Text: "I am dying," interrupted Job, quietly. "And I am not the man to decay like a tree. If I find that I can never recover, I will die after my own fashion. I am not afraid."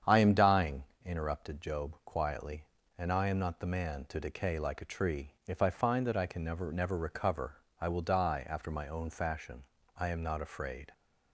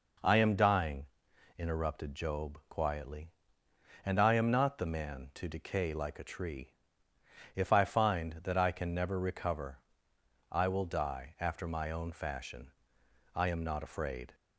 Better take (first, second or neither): second